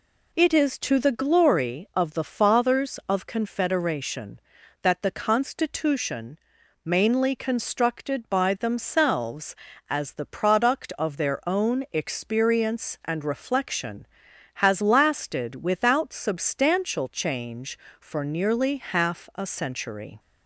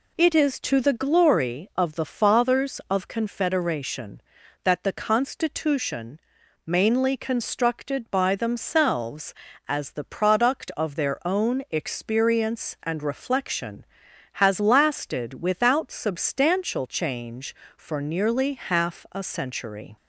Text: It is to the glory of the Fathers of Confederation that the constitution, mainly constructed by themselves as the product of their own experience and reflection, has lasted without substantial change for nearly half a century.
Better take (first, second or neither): neither